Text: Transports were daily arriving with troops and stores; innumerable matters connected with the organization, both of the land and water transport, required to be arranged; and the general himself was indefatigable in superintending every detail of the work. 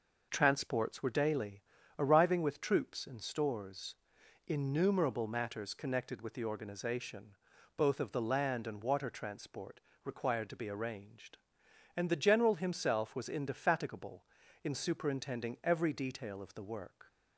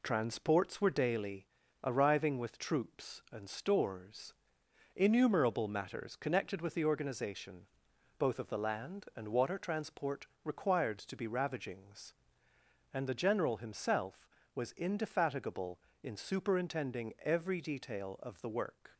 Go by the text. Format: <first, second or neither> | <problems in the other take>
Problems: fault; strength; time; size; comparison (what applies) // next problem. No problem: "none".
first | pauses between "daily" and "arriving"; at 1.4 s; 0.38 s long; slight in the first // says "ravagings" for "arranged"; at 11.2 s